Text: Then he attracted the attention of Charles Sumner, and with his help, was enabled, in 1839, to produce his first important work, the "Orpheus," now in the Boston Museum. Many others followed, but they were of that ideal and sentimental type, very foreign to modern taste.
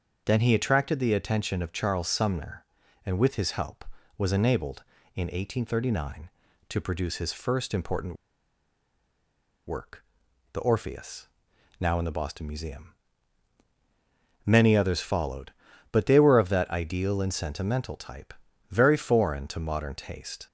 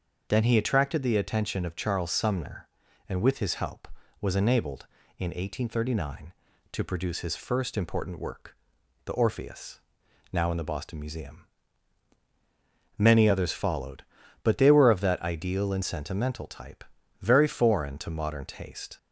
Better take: second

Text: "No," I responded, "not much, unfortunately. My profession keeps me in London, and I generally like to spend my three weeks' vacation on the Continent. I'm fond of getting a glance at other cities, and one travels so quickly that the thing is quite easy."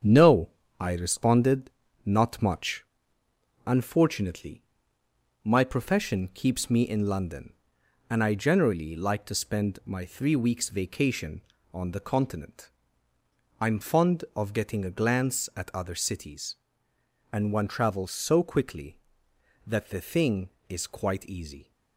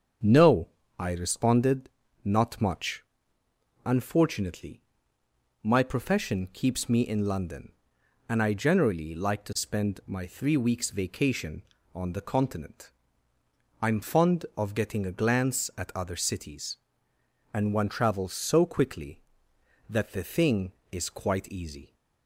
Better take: second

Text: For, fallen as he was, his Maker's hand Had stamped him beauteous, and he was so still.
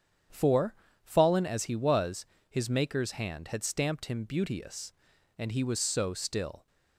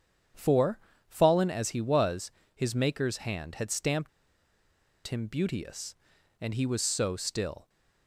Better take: first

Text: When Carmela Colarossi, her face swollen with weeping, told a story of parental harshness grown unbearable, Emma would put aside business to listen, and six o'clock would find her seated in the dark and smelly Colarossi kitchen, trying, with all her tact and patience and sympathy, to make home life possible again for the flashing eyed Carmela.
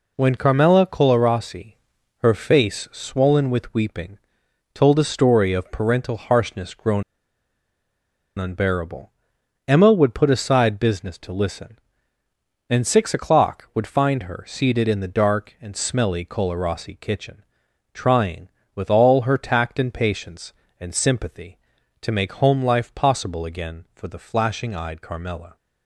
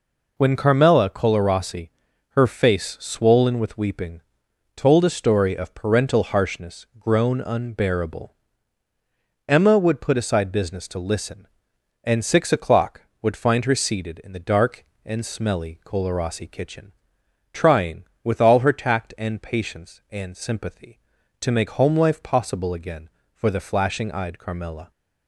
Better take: second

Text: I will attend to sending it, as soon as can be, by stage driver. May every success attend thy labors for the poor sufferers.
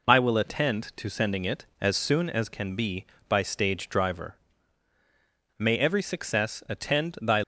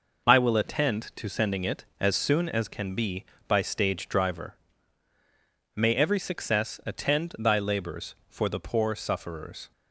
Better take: second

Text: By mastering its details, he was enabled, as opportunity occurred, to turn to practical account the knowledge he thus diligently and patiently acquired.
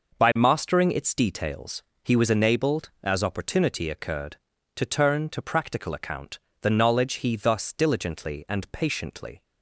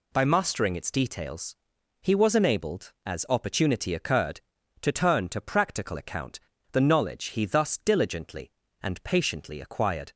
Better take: second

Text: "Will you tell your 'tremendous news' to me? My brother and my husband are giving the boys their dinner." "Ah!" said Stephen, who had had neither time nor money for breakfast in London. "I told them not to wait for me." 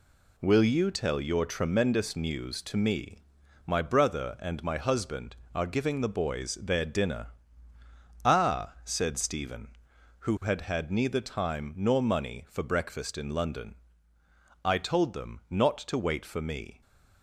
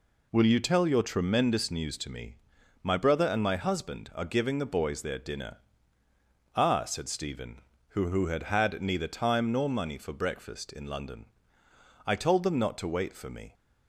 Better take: first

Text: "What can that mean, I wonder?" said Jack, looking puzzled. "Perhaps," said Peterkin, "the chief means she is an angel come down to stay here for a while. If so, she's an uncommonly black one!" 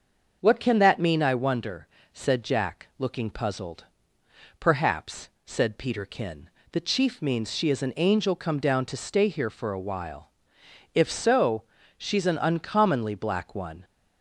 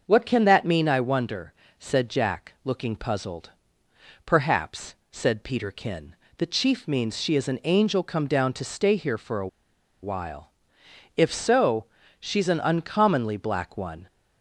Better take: first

